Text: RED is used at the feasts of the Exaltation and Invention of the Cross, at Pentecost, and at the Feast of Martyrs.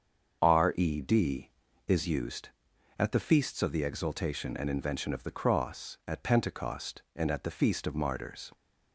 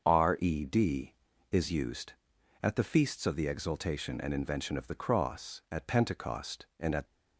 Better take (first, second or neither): first